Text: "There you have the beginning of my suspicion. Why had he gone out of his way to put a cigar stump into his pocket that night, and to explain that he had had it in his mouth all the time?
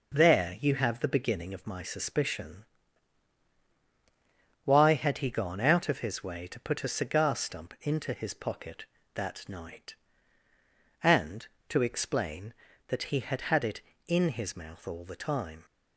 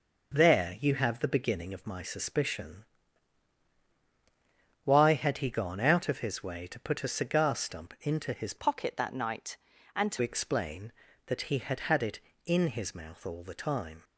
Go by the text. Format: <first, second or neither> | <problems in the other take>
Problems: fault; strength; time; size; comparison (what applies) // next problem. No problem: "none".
first | changes voice from "pocket" to "to"; from 8.5 to 10.2 s; 1.7 s long